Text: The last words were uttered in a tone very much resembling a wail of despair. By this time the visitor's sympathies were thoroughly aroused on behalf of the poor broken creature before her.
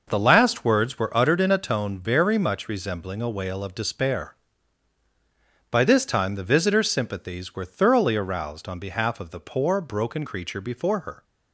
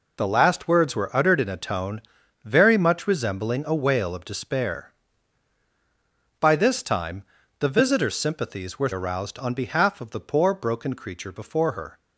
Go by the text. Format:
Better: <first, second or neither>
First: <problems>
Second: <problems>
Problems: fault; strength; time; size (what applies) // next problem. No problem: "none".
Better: first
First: none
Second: pauses between "tone" and "very"; at 2.0 s; 0.42 s long // pauses between "time" and "the"; slight; at 7.2 s; 0.36 s long // skips "thoroughly"; at 8.9 s